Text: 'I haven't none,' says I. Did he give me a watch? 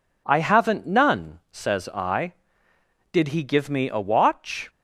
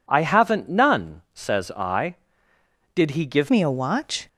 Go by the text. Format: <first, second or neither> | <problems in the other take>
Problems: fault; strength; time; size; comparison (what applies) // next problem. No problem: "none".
first | changes voice at "me"; from 3.4 s on; 0.8 s long